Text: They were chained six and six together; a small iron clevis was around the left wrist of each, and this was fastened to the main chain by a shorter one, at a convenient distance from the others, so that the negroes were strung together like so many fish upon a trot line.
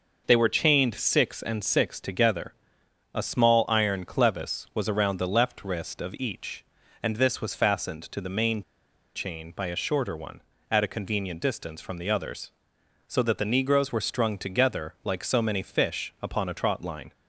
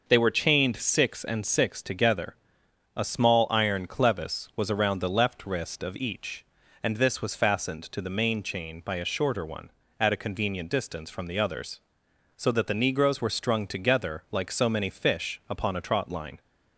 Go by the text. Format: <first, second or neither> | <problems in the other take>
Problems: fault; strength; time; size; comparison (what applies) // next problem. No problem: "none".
second | pauses between "main" and "chain"; noticeable; at 8.6 s; 0.53 s long